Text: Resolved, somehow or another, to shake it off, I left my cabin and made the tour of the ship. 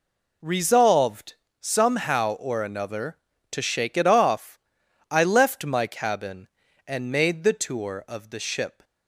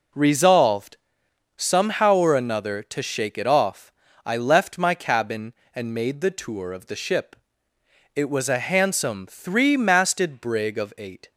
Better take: first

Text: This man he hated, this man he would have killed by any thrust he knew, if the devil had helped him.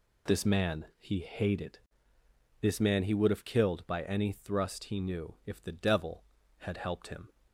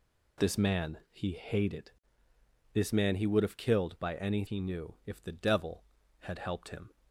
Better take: first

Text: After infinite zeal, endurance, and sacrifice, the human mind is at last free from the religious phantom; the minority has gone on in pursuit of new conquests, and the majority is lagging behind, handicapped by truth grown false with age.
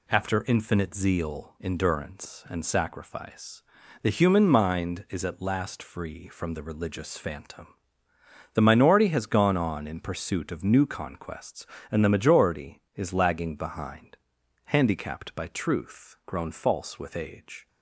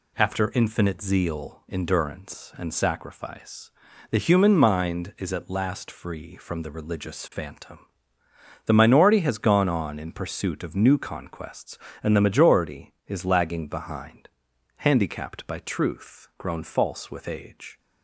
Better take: neither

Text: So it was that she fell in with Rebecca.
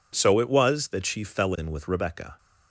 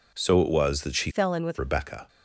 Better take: first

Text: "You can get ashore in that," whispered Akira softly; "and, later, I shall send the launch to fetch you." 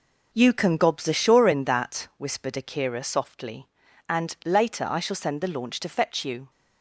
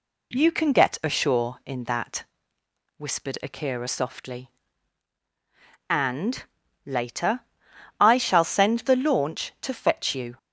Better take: second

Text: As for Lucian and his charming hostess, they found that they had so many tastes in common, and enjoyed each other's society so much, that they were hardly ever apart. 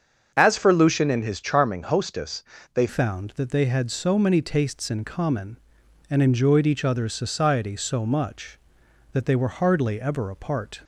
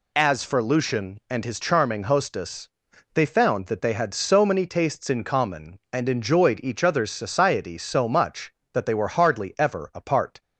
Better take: second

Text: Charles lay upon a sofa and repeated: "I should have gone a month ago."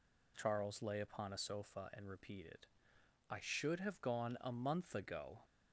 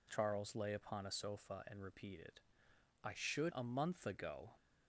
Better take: first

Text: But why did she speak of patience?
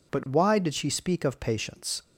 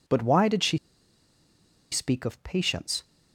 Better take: first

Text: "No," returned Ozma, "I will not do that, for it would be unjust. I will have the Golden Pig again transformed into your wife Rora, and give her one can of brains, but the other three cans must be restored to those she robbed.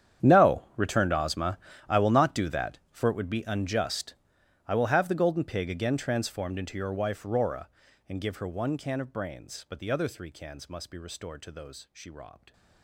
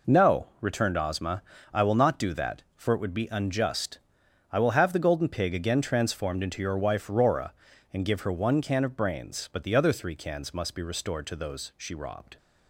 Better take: second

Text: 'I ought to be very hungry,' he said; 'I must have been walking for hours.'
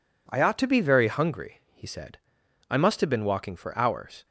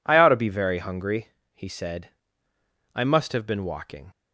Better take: first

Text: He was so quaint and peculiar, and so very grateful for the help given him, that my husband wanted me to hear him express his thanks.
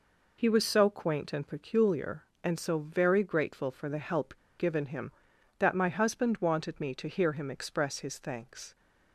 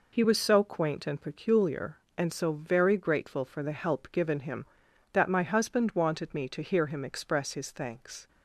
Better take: second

